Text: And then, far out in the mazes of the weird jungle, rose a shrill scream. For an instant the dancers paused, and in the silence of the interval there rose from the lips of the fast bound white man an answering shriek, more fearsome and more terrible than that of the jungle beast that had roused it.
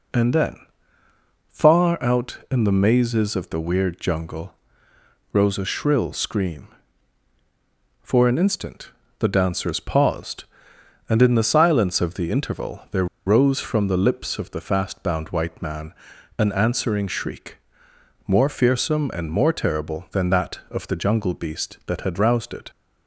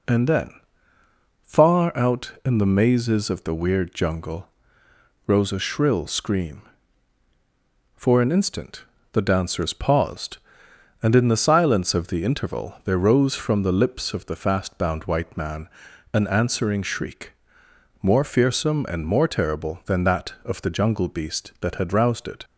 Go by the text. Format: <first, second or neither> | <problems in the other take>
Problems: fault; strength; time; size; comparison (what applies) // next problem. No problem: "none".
second | pauses between "instant" and "the"; slight; at 8.9 s; 0.28 s long; slight in the second // pauses between "there" and "rose"; slight; at 13.0 s; 0.20 s long // pauses between "man" and "an"; noticeable; at 15.9 s; 0.46 s long; noticeable in the second